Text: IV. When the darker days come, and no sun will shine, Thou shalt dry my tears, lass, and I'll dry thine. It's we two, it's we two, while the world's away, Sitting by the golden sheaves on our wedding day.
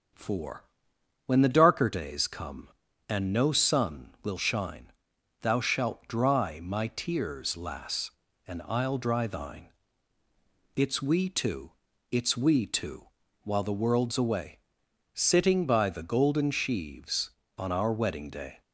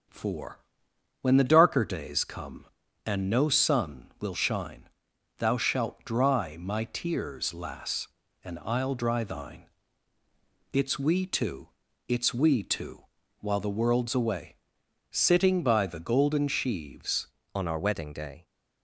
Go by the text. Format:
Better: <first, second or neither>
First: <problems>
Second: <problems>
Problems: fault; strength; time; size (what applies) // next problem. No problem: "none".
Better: first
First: starts louder than the rest; until 1.7 s; 7 dB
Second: starts louder than the rest; until 1.7 s; 7 dB // changes voice at "on"; from 17.5 s on; 0.9 s long